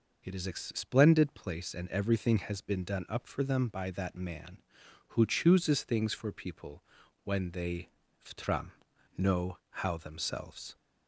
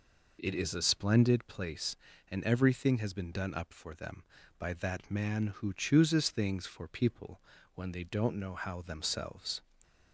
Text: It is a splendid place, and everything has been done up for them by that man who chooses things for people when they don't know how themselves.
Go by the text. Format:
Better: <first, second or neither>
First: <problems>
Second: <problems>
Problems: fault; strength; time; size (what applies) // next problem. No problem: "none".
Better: second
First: pauses between "people" and "when"; at 6.8 s; 0.44 s long // says "ftram" for "don't"; at 8.2 s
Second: pauses between "people" and "when"; slight; at 7.4 s; 0.32 s long